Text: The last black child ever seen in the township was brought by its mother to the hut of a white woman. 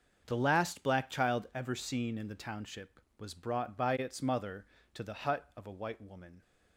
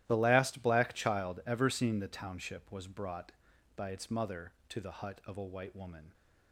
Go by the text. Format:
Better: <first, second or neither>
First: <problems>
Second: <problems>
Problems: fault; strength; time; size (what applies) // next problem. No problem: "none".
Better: first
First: starts louder than the rest; until 1.2 s; 6.5 dB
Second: starts louder than the rest; strong; until 1.0 s; 14 dB // skips "in"; at 1.9 s